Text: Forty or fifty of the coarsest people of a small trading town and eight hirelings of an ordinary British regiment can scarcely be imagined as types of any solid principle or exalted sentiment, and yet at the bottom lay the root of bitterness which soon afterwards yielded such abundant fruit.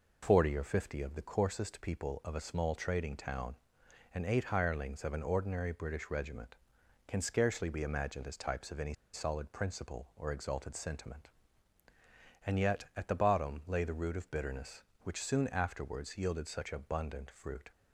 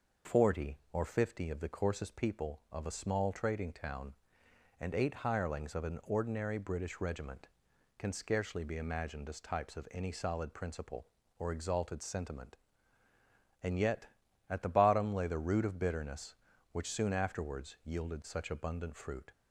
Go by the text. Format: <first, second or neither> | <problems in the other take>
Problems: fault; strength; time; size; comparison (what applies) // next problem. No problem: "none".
second | pauses between "any" and "solid"; slight; at 8.9 s; 0.19 s long